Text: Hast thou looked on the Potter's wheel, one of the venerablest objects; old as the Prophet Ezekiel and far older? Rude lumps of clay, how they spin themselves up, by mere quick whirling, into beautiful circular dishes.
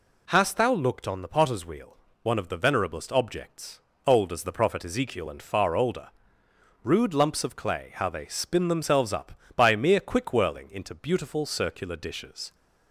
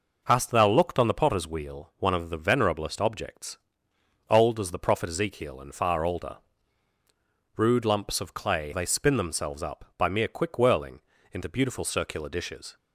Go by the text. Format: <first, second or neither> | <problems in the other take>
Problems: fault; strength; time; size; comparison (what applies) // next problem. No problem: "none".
first | skips "how"; at 8.7 s